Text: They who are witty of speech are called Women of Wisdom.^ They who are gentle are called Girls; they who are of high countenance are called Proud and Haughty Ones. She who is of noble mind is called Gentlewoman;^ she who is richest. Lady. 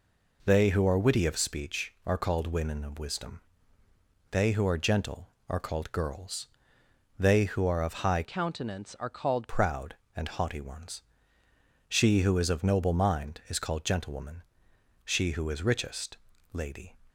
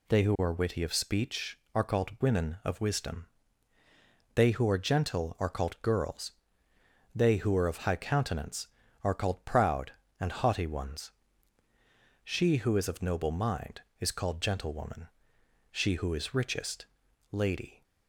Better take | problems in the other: second | changes voice from "countenance" to "called"; from 8.2 to 9.5 s; 1.3 s long

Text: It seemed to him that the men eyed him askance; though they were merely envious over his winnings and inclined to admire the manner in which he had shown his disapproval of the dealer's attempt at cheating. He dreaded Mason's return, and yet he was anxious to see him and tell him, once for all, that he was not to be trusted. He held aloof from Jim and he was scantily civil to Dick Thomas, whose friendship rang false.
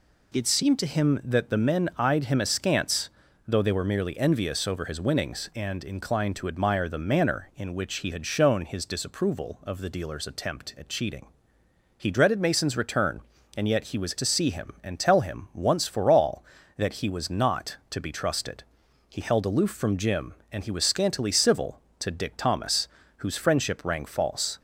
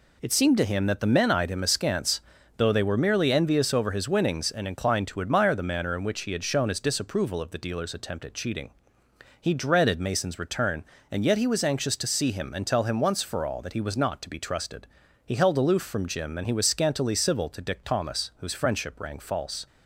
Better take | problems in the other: second | skips "anxious"; at 14.1 s

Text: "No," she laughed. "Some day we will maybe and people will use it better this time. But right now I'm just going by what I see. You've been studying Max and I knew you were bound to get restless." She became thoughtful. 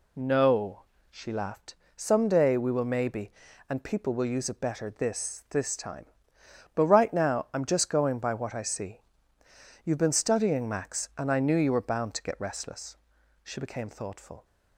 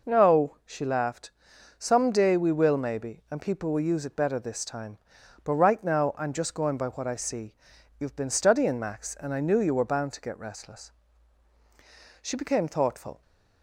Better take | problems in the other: second | says "this" twice; at 5.4 s

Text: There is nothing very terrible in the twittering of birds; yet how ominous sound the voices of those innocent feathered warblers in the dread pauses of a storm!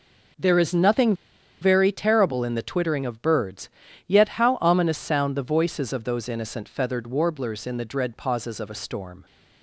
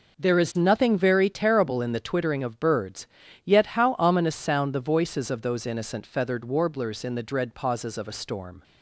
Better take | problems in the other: second | pauses between "nothing" and "very"; noticeable; at 1.1 s; 0.47 s long

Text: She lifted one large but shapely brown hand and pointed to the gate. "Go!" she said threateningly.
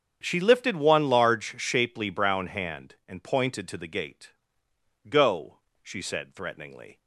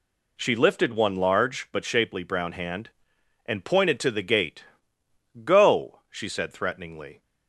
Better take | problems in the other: second | starts louder than the rest; strong; until 1.2 s; 7.5 dB // skips "but"; at 1.5 s

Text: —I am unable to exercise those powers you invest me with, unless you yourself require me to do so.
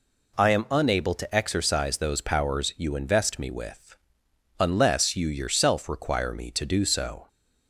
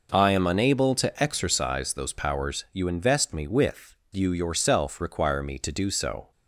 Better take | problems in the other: first | skips "unless"; at 4.0 s

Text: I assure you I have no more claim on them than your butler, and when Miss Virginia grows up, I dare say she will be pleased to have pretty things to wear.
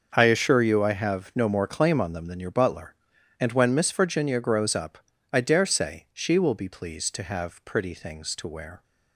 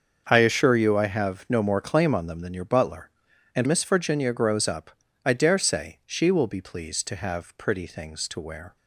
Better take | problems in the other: first | starts louder than the rest; until 1.2 s; 6.5 dB; also in the first // skips "when"; at 3.6 s

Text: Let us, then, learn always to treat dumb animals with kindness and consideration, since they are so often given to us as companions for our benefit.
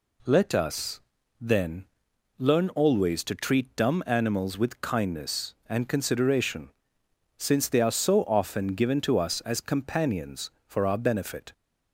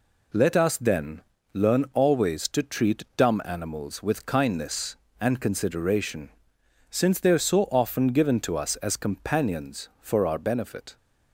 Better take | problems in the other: neither | none

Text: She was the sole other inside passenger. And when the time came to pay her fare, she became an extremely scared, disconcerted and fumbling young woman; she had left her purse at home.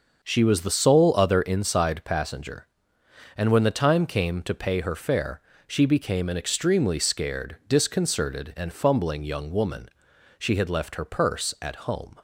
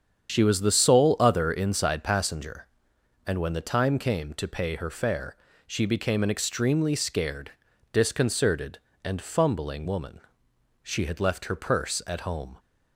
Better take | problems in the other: first | starts louder than the rest; strong; until 1.3 s; 8 dB; also in the first // skips "young"; at 9.8 s

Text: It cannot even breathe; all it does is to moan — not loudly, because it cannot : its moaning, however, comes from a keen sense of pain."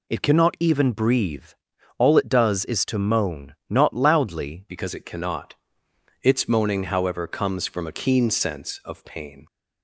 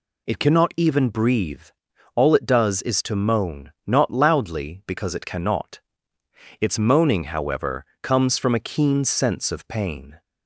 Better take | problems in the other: second | changes voice at "because"; from 4.6 s on; 4.8 s long

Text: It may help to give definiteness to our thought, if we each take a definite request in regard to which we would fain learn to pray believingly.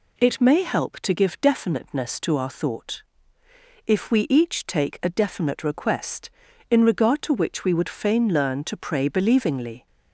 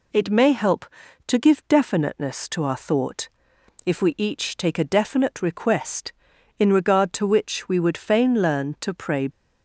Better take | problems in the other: first | stops before "believingly"; at 9.3 s

